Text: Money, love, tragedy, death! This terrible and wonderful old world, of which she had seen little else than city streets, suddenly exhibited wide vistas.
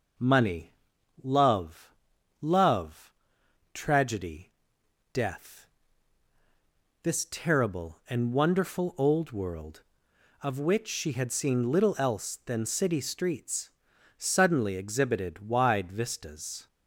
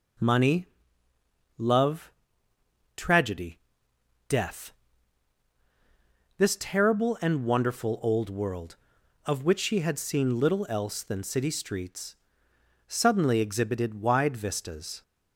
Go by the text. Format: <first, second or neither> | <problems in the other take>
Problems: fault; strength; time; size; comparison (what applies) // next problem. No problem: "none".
second | says "love" twice; at 2.4 s